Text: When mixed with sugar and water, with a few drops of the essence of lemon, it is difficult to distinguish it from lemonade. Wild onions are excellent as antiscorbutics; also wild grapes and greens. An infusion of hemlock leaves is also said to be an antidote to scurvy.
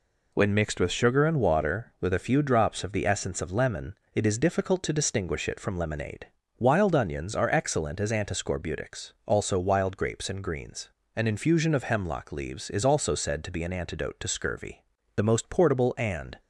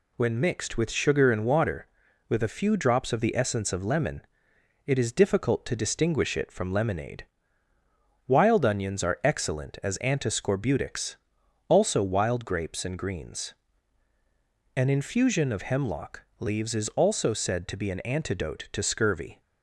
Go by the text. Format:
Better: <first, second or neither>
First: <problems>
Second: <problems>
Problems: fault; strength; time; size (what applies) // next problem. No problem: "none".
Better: second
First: goes on to say "The most portable and"; noticeable; from 15.1 s on; 1.2 s long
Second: none